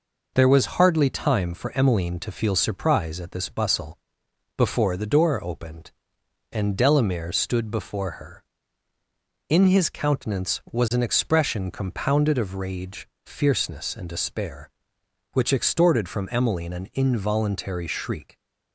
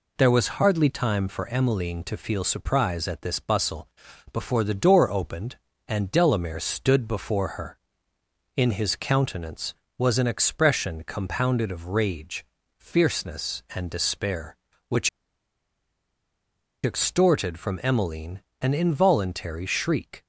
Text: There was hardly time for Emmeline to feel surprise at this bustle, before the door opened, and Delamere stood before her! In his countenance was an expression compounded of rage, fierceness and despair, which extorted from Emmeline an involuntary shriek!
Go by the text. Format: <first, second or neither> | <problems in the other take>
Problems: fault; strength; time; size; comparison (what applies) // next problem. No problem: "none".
first | pauses between "which" and "extorted"; strong; at 15.0 s; 1.7 s long // pauses between "Emmeline" and "an"; slight; at 18.4 s; 0.20 s long